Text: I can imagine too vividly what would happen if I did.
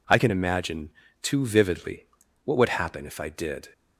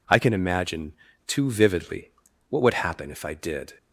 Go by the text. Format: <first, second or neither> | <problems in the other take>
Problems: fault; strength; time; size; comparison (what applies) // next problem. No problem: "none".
neither | pauses between "imagine" and "too"; slight; the same in both // pauses between "vividly" and "what"; the same in both